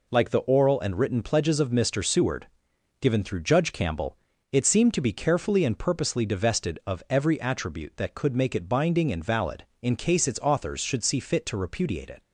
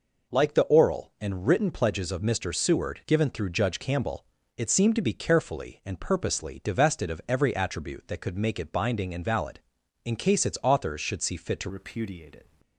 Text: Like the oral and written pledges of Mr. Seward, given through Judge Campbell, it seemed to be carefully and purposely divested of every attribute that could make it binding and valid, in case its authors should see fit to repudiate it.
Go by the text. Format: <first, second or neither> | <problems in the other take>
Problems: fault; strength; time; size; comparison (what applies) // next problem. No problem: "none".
first | changes voice at "repudiate"; from 11.6 s on; 0.8 s long